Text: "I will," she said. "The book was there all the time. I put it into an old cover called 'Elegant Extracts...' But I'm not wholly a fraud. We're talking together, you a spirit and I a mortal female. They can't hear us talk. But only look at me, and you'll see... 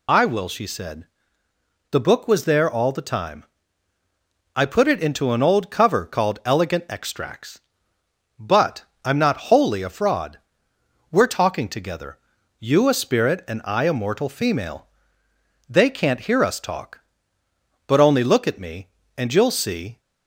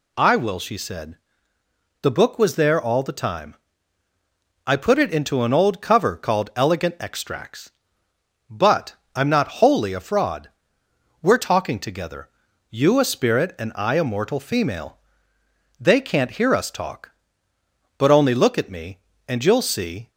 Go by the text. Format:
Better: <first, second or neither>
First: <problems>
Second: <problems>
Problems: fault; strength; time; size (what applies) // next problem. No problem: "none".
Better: second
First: loses the start of "I"; at 0.0 s; 30 ms // pauses between "But" and "I'm"; slight; at 8.8 s; 0.20 s long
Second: pauses between "But" and "I'm"; slight; at 8.9 s; 0.20 s long